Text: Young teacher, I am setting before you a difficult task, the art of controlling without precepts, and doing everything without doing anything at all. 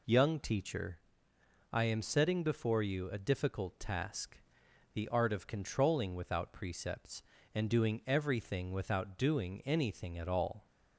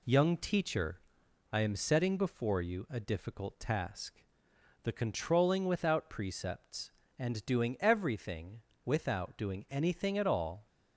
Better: first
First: none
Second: skips "art of"; at 4.9 s // pauses between "everything" and "without"; slight; at 8.5 s; 0.26 s long

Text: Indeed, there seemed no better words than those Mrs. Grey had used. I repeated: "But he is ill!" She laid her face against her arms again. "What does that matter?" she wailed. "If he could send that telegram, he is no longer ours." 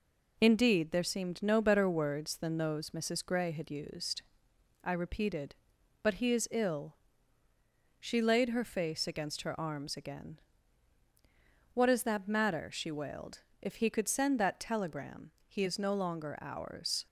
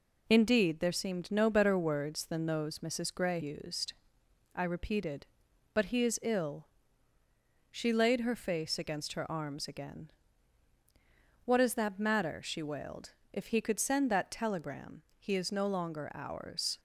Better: first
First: none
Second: skips "had"; at 3.4 s

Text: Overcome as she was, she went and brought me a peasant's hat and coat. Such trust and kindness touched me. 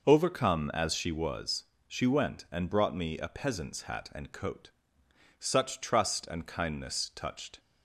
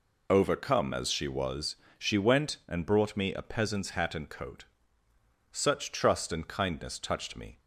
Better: second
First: stops before "me"; at 7.5 s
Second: none

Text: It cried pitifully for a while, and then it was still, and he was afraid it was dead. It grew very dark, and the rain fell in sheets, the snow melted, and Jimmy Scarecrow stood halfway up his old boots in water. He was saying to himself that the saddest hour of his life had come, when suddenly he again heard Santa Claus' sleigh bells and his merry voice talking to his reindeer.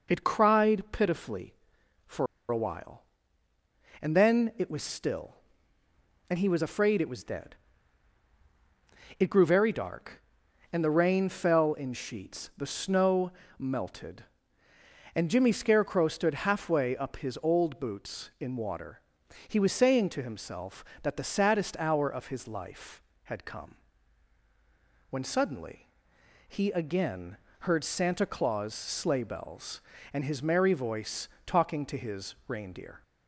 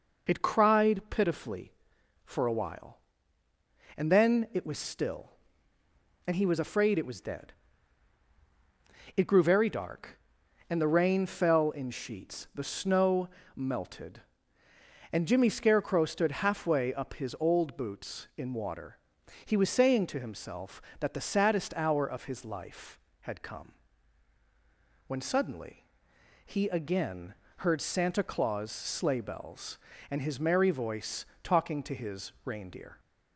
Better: second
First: pauses between "for" and "a"; slight; at 2.2 s; 0.23 s long // pauses between "snow" and "melted"; slight; at 13.2 s; 0.28 s long // pauses between "suddenly" and "he"; noticeable; at 25.8 s; 0.58 s long // pauses between "again" and "heard"; slight; at 27.3 s; 0.24 s long // pauses between "voice" and "talking"; slight; at 31.2 s; 0.18 s long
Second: pauses between "snow" and "melted"; slight; at 13.2 s; 0.28 s long // pauses between "suddenly" and "he"; noticeable; at 25.8 s; 0.58 s long // pauses between "again" and "heard"; slight; at 27.3 s; 0.24 s long // pauses between "voice" and "talking"; slight; at 31.2 s; 0.18 s long

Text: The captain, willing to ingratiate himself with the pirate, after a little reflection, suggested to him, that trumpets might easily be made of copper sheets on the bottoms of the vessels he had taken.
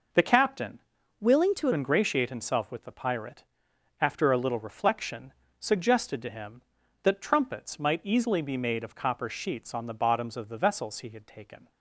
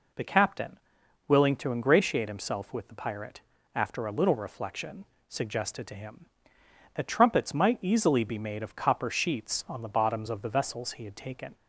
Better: second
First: changes voice from "willing" to "to"; from 1.1 to 1.6 s; 0.5 s long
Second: none

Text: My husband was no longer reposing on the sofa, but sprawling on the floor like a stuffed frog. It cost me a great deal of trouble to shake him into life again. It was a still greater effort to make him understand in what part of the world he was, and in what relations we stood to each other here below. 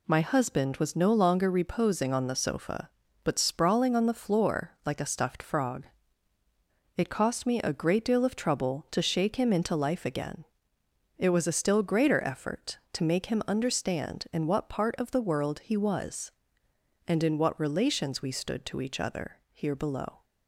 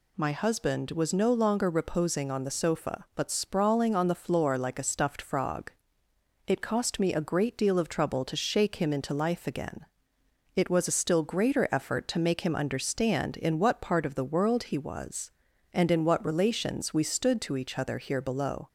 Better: neither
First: none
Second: none

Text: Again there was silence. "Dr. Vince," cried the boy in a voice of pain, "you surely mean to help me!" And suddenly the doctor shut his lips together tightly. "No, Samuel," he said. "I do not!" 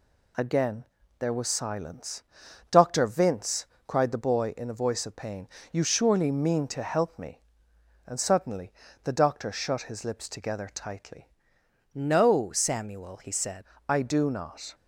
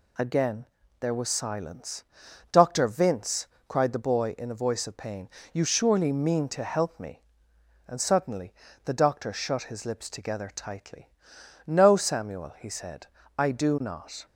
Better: second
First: pauses between "Again" and "there"; slight; at 0.8 s; 0.36 s long // pauses between "suddenly" and "the"; slight; at 8.7 s; 0.32 s long // changes voice from "No" to "said"; from 11.9 to 13.6 s; 1.7 s long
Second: pauses between "Again" and "there"; slight; at 0.6 s; 0.36 s long // pauses between "suddenly" and "the"; slight; at 8.5 s; 0.32 s long

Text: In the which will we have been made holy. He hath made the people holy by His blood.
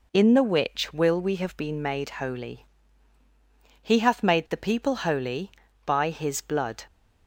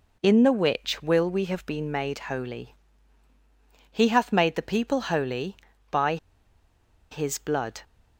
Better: first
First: none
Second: pauses between "by" and "His"; noticeable; at 6.1 s; 0.94 s long

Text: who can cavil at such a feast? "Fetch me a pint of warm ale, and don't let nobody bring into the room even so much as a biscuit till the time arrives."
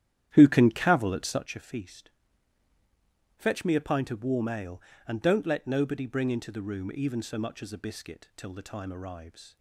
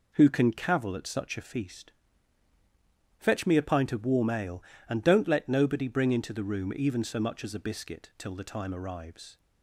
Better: second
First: starts louder than the rest; strong; until 1.5 s; 11 dB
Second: none

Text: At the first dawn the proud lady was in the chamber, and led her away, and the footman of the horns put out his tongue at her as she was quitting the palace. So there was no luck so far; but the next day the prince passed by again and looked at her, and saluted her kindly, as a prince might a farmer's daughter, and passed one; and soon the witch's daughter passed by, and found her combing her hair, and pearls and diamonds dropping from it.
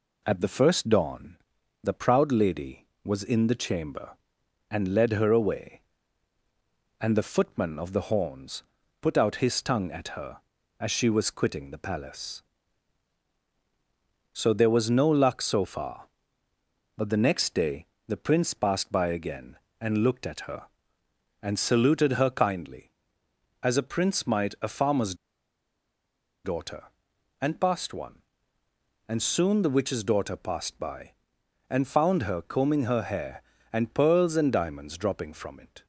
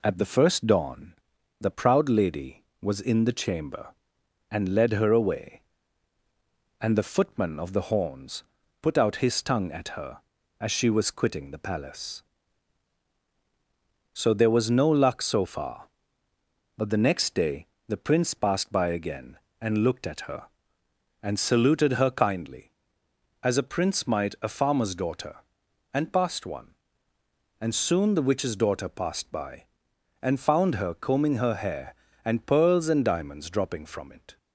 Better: second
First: pauses between "dawn" and "the"; noticeable; at 1.3 s; 0.48 s long // pauses between "horns" and "put"; at 8.6 s; 0.38 s long // pauses between "day" and "the"; slight; at 17.8 s; 0.20 s long // pauses between "farmer's" and "daughter"; strong; at 25.1 s; 1.2 s long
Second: pauses between "dawn" and "the"; noticeable; at 1.1 s; 0.48 s long // pauses between "horns" and "put"; at 8.4 s; 0.38 s long // pauses between "day" and "the"; slight; at 17.6 s; 0.20 s long

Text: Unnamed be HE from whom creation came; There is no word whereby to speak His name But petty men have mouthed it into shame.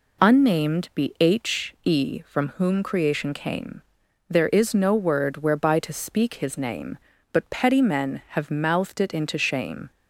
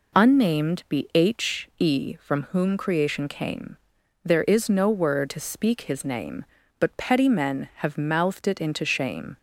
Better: first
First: none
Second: skips "whereby"; at 5.2 s

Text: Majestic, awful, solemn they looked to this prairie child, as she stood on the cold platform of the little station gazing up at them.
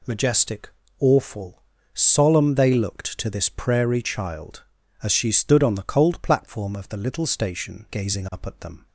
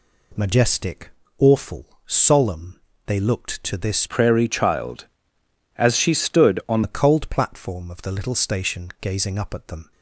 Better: first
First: none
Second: pauses between "solemn" and "they"; slight; at 2.8 s; 0.24 s long // changes voice from "prairie" to "on"; from 4.0 to 6.8 s; 2.8 s long

